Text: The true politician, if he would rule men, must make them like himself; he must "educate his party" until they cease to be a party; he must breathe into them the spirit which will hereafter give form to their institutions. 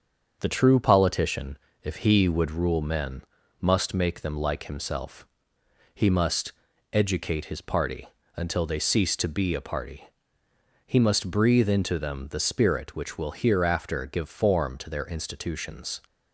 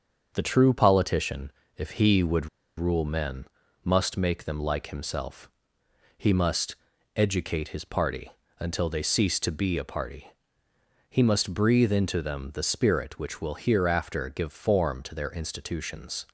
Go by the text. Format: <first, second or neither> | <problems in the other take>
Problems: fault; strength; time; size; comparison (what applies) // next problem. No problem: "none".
first | starts louder than the rest; until 1.3 s; 6.5 dB; also in the first // pauses between "would" and "rule"; slight; at 2.4 s; 0.30 s long // pauses between "must" and "educate"; at 6.7 s; 0.42 s long; also in the first // pauses between "party" and "until"; slight; at 8.3 s; 0.28 s long; slight in the first